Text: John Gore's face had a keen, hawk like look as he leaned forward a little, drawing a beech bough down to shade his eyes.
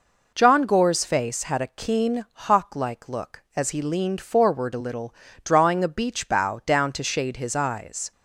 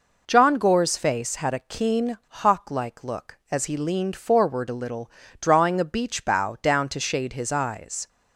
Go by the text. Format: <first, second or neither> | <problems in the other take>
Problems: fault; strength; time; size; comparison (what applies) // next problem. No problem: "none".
neither | none